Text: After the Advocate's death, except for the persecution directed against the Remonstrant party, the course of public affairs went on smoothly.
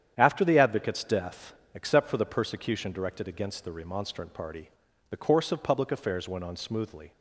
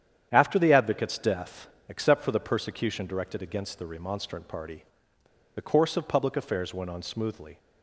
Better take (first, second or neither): first